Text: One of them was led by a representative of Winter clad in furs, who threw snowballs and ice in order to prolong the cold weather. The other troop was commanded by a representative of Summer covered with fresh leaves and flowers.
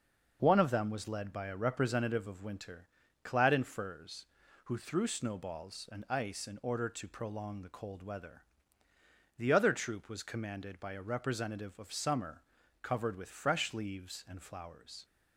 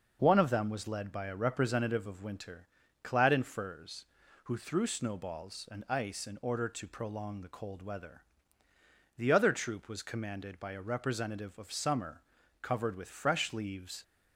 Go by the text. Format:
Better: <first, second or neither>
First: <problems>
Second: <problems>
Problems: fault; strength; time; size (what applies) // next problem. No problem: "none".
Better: first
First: pauses between "Winter" and "clad"; slight; at 2.8 s; 0.36 s long // pauses between "Summer" and "covered"; at 12.4 s; 0.40 s long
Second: pauses between "Winter" and "clad"; slight; at 2.6 s; 0.36 s long // pauses between "Summer" and "covered"; at 12.2 s; 0.40 s long // stops before "and flowers"; at 14.0 s